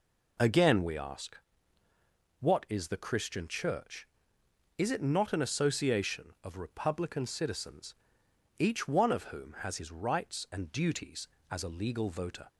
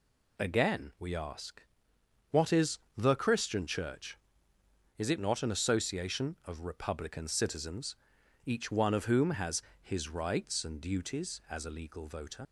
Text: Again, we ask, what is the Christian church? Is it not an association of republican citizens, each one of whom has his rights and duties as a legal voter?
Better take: first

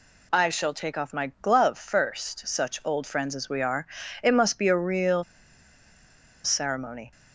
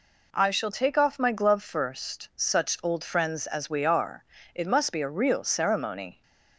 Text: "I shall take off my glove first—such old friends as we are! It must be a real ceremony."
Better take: second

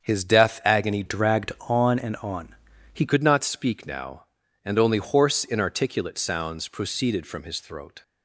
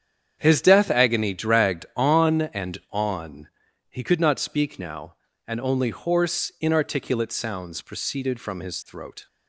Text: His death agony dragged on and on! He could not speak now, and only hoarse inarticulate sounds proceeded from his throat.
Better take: second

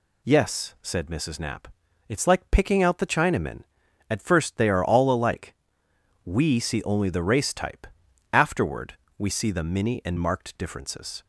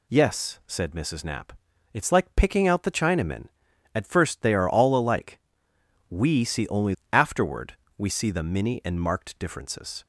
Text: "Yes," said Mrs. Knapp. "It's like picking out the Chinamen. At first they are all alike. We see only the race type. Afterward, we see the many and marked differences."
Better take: first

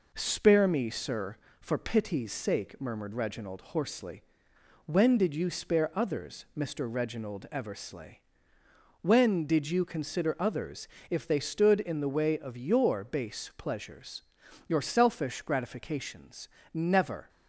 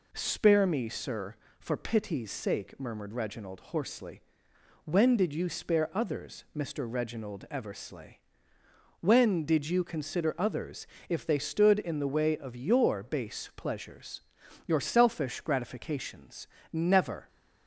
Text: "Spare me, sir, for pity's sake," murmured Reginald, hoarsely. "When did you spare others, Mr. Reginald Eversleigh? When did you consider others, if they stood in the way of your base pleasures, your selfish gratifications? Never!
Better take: second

